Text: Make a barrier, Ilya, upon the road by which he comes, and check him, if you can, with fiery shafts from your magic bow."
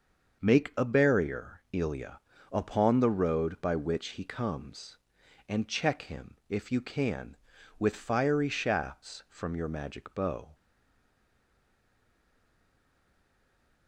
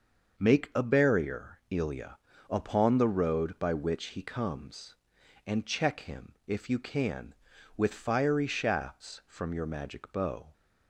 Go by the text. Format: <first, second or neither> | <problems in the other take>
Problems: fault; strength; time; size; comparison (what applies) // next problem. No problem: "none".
second | starts louder than the rest; until 1.4 s; 6 dB; also in the second // stays silent after the last word; strong; from 10.5 s on; 3.3 s long